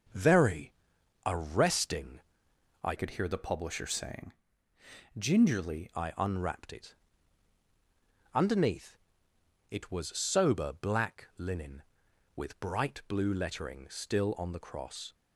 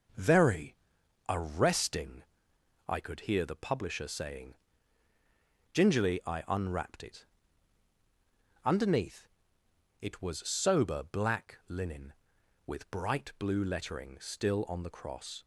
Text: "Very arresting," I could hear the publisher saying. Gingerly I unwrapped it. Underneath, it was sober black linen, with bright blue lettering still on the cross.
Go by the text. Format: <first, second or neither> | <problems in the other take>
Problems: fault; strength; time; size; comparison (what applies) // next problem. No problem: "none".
second | starts louder than the rest; until 1.6 s; 6 dB // pauses between "Very" and "arresting"; noticeable; at 0.7 s; 0.54 s long; noticeable in the second // changes voice from "could" to "Gingerly"; from 2.9 to 5.8 s; 2.9 s long